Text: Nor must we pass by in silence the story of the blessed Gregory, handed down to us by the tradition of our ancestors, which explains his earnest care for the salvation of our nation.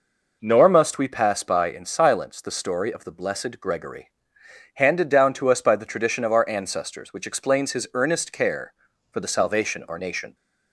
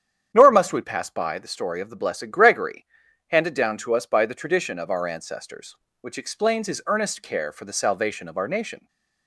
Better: first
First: none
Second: starts louder than the rest; strong; until 1.3 s; 9 dB // skips "in silence"; at 1.3 s

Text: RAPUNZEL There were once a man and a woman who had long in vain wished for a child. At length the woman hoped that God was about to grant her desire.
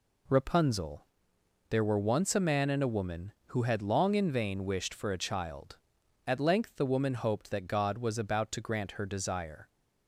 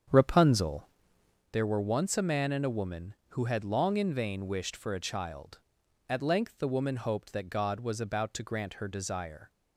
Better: first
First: pauses between "RAPUNZEL" and "There"; noticeable; at 1.0 s; 0.62 s long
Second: starts louder than the rest; strong; until 1.4 s; 8 dB // pauses between "RAPUNZEL" and "There"; noticeable; at 0.8 s; 0.62 s long

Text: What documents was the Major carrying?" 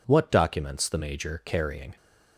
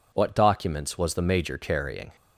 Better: second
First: skips "was"; at 0.8 s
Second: none

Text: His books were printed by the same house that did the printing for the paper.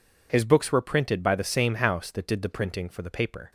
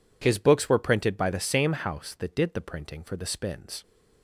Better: first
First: none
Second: says "spins" for "paper"; at 3.2 s

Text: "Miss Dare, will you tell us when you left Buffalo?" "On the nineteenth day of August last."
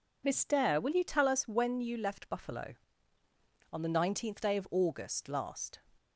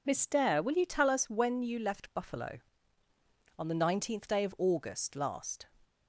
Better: neither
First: none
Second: none

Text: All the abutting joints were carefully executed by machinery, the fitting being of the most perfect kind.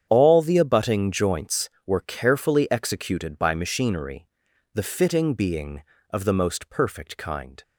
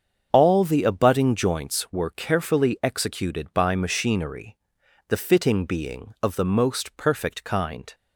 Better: neither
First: starts louder than the rest; strong; until 1.1 s; 8.5 dB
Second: starts louder than the rest; strong; until 1.3 s; 7.5 dB

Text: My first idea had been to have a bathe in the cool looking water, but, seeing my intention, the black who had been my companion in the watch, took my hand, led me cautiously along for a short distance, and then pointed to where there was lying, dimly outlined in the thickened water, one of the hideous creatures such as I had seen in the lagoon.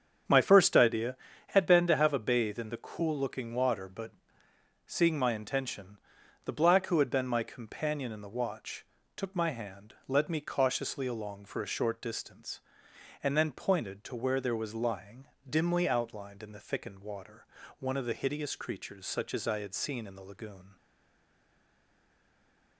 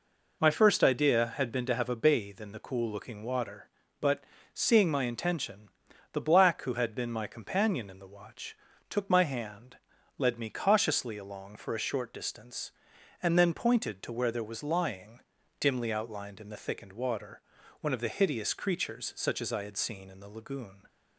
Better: second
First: starts louder than the rest; strong; until 1.6 s; 7.5 dB // stays silent after the last word; noticeable; from 20.7 s on; 2.0 s long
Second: none

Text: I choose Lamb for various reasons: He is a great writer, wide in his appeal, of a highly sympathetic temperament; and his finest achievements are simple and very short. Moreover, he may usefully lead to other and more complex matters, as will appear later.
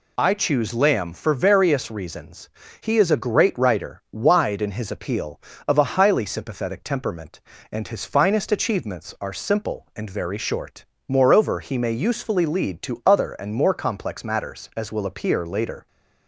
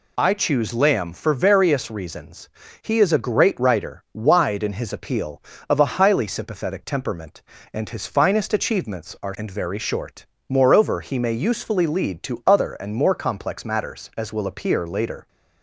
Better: first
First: none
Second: skips "simple"; at 9.3 s

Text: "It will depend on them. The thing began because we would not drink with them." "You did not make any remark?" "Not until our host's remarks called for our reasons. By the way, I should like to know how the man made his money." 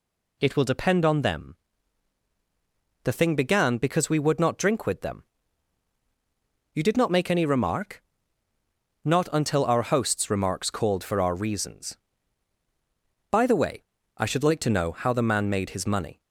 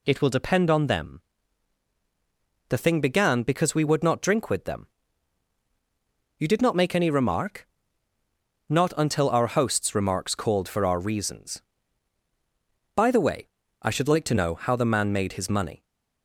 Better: neither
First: none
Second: none

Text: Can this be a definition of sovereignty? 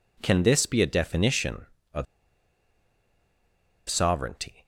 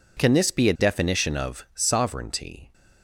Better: second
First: pauses between "of" and "sovereignty"; strong; at 2.0 s; 1.8 s long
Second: none

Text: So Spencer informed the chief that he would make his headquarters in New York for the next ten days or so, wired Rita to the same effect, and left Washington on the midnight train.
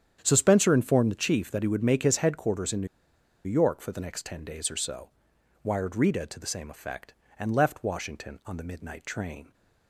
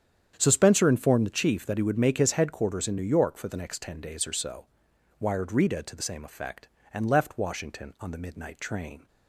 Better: second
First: starts louder than the rest; strong; until 1.2 s; 9 dB // pauses between "New" and "York"; noticeable; at 2.8 s; 0.59 s long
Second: starts louder than the rest; strong; until 1.3 s; 9 dB

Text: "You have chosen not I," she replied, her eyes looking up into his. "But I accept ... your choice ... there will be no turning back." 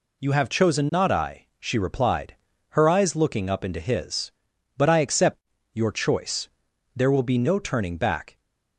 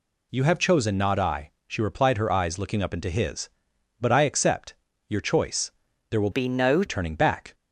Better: first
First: none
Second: changes voice from "be" to "no"; from 6.3 to 6.8 s; 0.5 s long

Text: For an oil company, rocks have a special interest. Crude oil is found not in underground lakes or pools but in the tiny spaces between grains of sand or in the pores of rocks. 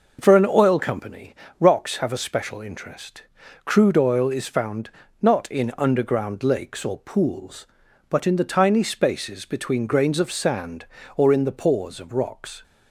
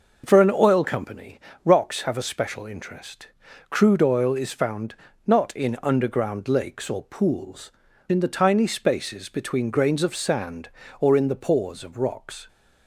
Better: first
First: pauses between "found" and "not"; slight; at 4.8 s; 0.32 s long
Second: pauses between "found" and "not"; slight; at 4.9 s; 0.32 s long // skips "but"; at 7.8 s

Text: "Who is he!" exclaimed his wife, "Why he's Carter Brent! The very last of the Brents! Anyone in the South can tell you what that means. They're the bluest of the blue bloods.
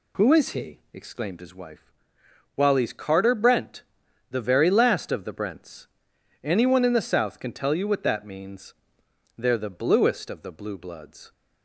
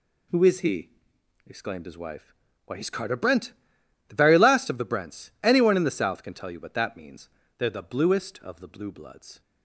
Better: second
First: says "While" for "Why"; at 2.5 s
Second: none

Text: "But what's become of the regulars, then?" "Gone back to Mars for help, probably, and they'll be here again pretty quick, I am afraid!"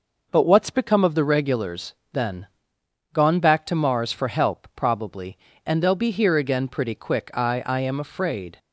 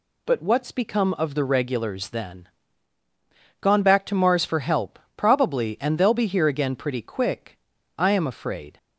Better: second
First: says "I" twice; at 7.6 s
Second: none

